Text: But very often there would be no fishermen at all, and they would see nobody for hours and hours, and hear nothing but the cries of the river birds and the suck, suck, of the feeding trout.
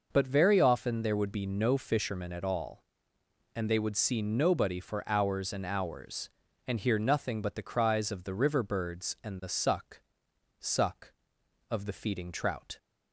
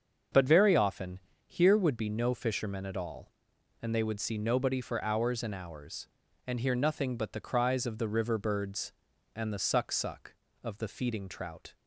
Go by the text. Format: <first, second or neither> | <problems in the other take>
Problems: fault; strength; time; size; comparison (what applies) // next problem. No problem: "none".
first | starts louder than the rest; until 1.5 s; 6.5 dB // says "here" for "there"; at 1.4 s